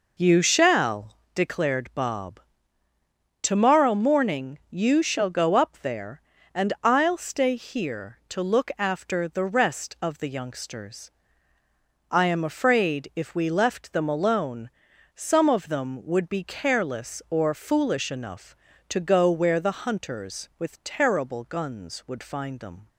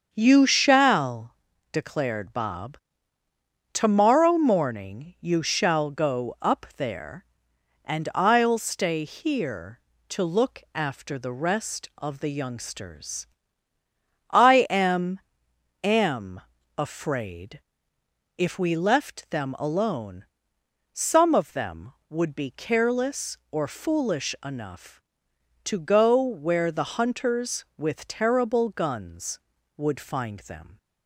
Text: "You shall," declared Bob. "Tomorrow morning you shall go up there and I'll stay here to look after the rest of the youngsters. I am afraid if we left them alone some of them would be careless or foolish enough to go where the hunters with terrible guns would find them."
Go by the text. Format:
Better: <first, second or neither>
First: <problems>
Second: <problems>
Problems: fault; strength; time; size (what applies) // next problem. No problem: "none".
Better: first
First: pauses between "alone" and "some"; at 14.7 s; 0.42 s long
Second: starts louder than the rest; until 1.1 s; 7 dB // says "am" twice; at 15.8 s // pauses between "afraid" and "if"; noticeable; at 17.6 s; 0.76 s long // pauses between "alone" and "some"; noticeable; at 20.2 s; 0.68 s long